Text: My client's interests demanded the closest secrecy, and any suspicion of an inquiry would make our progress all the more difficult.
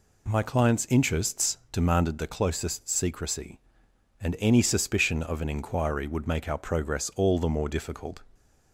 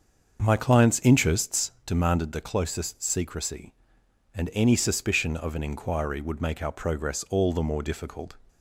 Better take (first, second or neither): first